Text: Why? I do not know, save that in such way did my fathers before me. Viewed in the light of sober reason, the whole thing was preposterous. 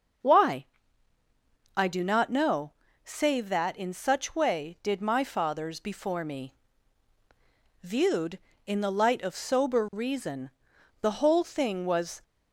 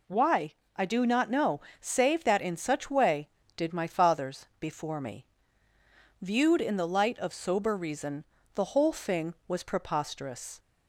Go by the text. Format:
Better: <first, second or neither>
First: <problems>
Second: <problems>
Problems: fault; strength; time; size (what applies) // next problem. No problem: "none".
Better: second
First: starts louder than the rest; until 2.3 s; 6.5 dB // stops before "preposterous"; at 12.2 s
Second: none